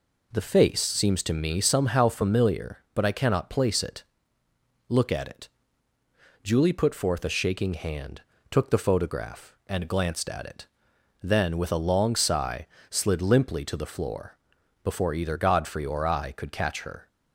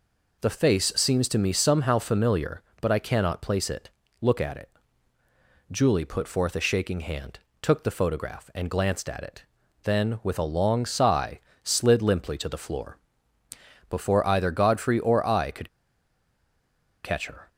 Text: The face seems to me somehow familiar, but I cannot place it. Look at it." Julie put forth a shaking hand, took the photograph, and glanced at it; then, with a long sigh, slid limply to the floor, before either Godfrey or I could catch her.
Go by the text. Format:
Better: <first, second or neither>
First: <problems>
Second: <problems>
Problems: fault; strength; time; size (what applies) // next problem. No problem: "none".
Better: first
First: none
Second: pauses between "could" and "catch"; strong; at 15.6 s; 1.3 s long